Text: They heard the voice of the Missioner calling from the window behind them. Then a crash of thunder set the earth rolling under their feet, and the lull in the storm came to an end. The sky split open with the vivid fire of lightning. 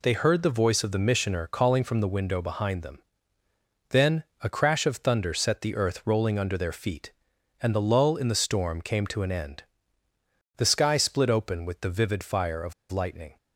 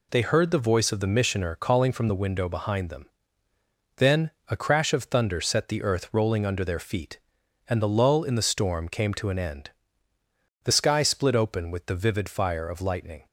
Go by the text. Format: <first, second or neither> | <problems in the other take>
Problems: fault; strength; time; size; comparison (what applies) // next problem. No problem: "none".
second | pauses between "Then" and "a"; slight; at 4.2 s; 0.18 s long; slight in the second // pauses between "of" and "lightning"; slight; at 12.7 s; 0.17 s long